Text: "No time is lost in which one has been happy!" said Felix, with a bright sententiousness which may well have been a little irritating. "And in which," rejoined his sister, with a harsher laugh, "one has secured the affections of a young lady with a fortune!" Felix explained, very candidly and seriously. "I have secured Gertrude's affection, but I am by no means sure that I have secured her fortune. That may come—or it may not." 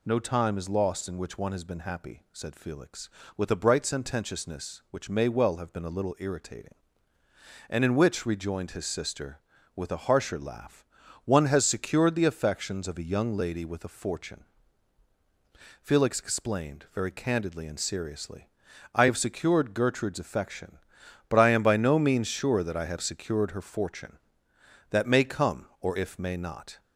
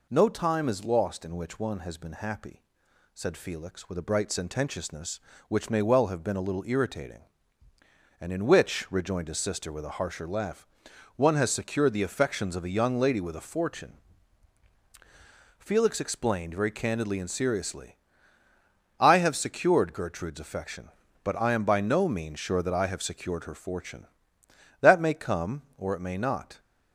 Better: second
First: says "if" for "it"; at 25.9 s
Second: none

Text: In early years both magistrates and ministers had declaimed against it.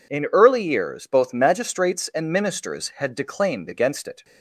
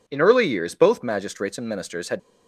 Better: first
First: none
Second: stops before "declaimed against it"; at 2.1 s

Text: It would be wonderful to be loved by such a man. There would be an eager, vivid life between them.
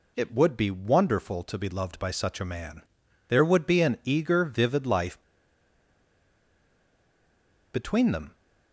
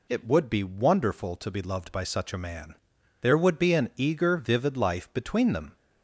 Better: second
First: pauses between "life" and "between"; strong; at 5.2 s; 2.5 s long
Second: none

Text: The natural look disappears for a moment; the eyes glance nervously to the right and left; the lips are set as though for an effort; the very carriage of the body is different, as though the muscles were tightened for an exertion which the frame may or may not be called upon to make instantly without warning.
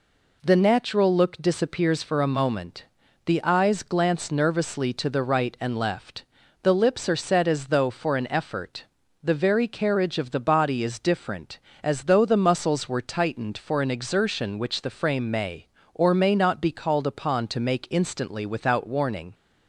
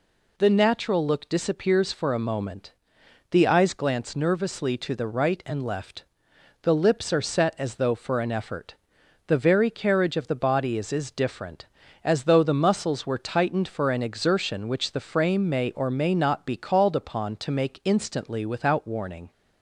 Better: first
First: none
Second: says "is" twice; at 10.9 s

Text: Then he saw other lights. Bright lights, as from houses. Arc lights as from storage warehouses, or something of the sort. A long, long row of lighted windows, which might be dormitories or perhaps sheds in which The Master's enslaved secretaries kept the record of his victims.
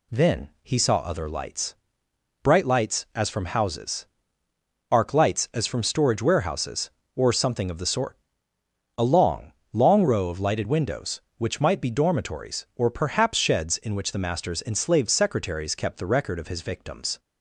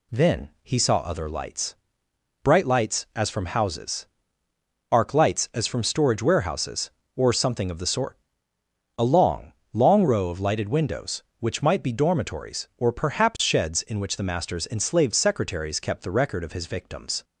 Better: neither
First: none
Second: none

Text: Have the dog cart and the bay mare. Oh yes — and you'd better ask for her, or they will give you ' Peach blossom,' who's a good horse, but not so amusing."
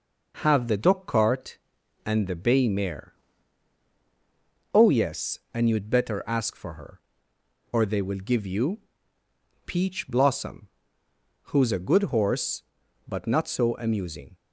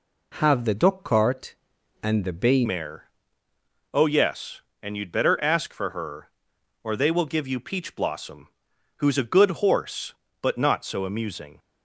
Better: first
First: none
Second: changes voice at "mare"; from 2.6 s on; 8.9 s long

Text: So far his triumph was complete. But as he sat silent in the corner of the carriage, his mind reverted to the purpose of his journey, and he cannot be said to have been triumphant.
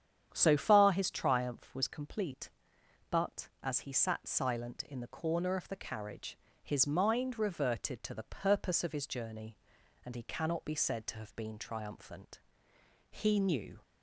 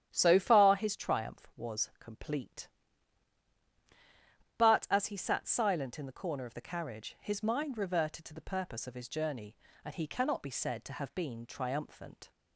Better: second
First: starts louder than the rest; strong; until 1.3 s; 9 dB // goes on to say "He knew"; noticeable; from 13.0 s on; 0.72 s long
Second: starts louder than the rest; strong; until 1.1 s; 10 dB

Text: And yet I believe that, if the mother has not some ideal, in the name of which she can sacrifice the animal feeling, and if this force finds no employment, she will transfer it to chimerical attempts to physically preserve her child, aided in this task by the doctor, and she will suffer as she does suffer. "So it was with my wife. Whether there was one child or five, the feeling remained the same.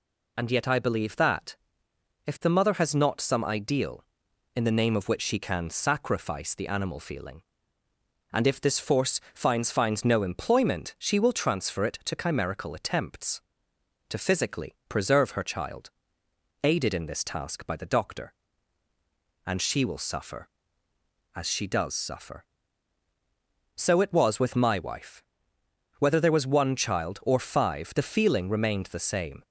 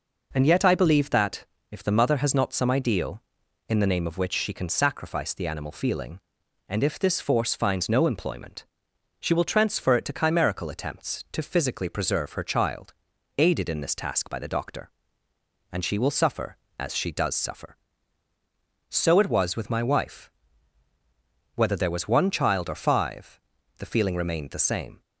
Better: second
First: says "finds" twice; at 9.7 s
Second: none

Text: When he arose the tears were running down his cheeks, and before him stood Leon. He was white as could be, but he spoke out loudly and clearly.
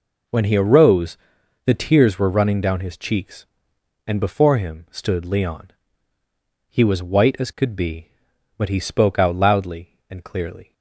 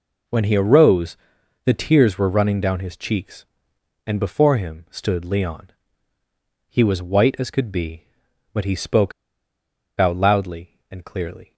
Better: first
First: pauses between "arose" and "the"; noticeable; at 1.1 s; 0.48 s long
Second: pauses between "arose" and "the"; noticeable; at 1.1 s; 0.48 s long // pauses between "spoke" and "out"; noticeable; at 9.1 s; 0.87 s long

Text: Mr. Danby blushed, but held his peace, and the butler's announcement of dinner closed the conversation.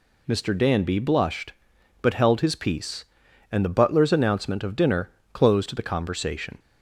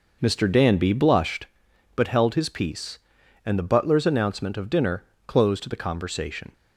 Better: first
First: pauses between "dinner" and "closed"; slight; at 5.0 s; 0.24 s long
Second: starts louder than the rest; noticeable; until 1.5 s; 5.5 dB // pauses between "dinner" and "closed"; slight; at 5.0 s; 0.24 s long

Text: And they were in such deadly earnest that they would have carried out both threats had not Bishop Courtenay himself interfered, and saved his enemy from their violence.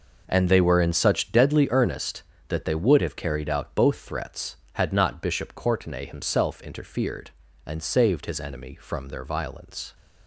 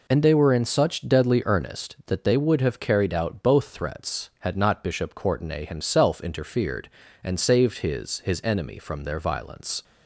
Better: first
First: none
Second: says "his" twice; at 8.1 s

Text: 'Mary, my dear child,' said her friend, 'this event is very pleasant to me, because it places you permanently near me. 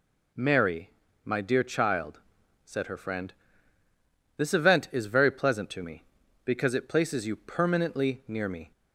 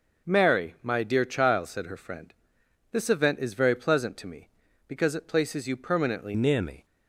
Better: first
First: none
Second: changes voice at "near"; from 6.3 s on; 0.5 s long

